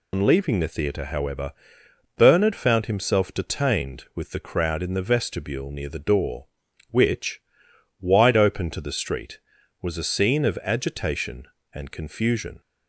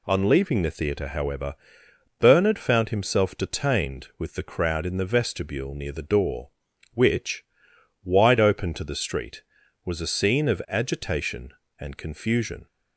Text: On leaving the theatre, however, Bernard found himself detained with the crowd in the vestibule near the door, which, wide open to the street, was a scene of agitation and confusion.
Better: second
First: loses the start of "On"; at 0.1 s; 100 ms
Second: none

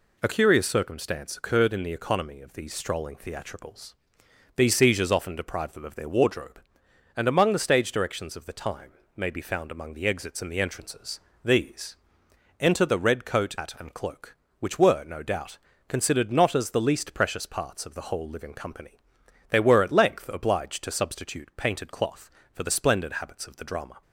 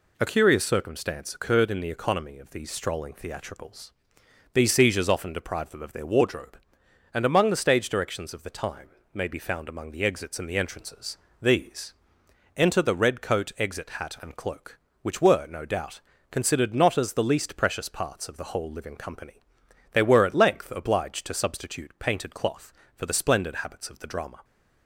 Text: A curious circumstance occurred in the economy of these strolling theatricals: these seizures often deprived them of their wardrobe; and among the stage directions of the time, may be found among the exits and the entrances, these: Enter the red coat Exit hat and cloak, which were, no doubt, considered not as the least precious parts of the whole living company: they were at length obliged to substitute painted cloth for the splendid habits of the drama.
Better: second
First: skips "Exit"; at 13.5 s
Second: none

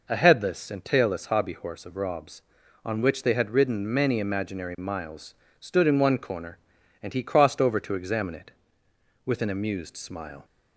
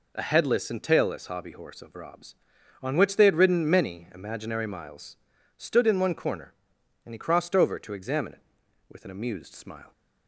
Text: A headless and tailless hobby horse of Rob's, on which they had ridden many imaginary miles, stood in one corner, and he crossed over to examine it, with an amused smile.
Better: neither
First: none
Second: none

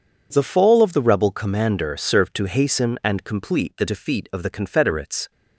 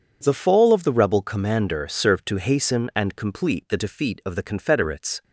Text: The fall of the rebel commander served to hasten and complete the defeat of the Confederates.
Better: neither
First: none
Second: none

